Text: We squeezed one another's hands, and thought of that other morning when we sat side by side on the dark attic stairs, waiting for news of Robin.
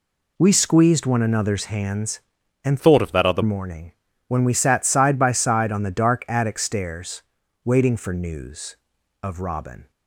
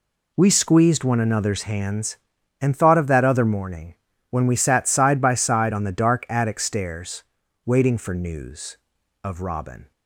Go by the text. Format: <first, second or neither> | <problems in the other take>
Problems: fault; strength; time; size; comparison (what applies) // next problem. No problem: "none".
second | changes voice from "thought" to "other"; from 2.7 to 3.4 s; 0.7 s long // pauses between "morning" and "when"; slight; at 3.9 s; 0.36 s long; slight in the second